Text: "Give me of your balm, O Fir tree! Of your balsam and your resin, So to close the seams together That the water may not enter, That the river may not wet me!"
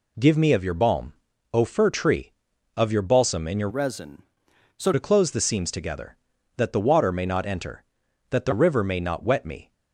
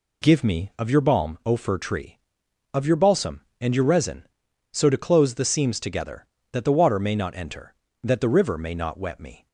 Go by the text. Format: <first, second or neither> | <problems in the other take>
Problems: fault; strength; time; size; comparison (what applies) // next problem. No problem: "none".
second | changes voice from "resin" to "So"; from 3.6 to 4.9 s; 1.3 s long